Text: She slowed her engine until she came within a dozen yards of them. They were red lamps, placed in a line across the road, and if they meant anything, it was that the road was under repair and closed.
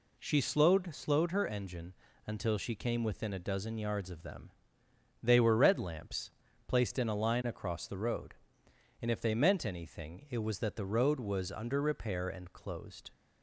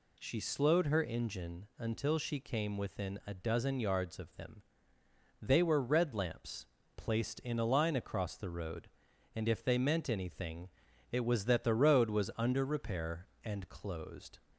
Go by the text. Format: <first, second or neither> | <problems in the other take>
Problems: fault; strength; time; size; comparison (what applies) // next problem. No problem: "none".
second | says "slowed" twice; at 0.9 s // pauses between "engine" and "until"; slight; at 1.9 s; 0.32 s long